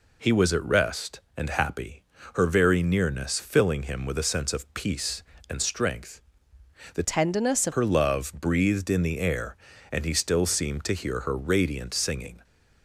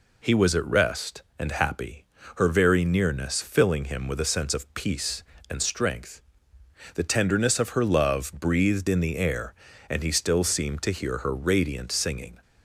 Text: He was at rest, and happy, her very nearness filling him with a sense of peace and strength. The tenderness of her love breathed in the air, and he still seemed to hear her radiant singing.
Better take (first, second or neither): second